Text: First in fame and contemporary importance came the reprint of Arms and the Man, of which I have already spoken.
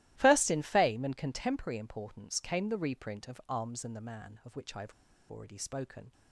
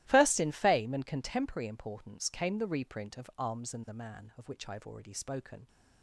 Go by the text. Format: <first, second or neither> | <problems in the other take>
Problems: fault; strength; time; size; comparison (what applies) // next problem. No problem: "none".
second | starts louder than the rest; strong; until 1.1 s; 15.5 dB; strong in the second // pauses between "have" and "already"; at 4.9 s; 0.39 s long